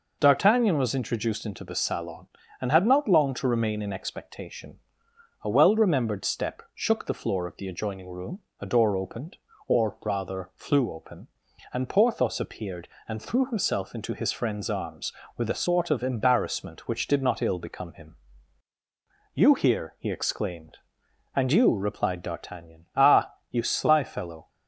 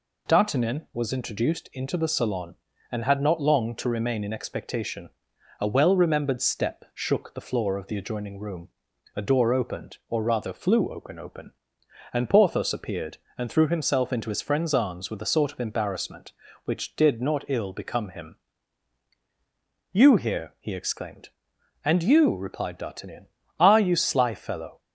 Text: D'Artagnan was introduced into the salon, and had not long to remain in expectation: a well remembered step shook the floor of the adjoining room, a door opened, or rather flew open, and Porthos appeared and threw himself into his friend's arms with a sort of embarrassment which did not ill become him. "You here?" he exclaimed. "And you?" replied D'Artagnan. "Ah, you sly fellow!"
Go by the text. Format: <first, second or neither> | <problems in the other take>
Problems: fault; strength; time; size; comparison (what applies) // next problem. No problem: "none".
first | says "open" twice; at 11.1 s